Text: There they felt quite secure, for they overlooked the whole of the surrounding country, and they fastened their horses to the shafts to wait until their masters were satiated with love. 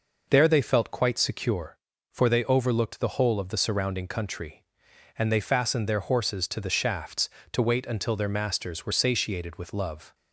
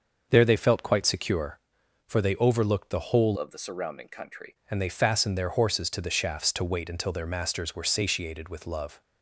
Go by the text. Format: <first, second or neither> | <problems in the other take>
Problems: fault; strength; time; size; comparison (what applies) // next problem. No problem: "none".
first | starts louder than the rest; until 1.3 s; 6.5 dB // changes voice from "of" to "country"; from 3.3 to 4.5 s; 1.2 s long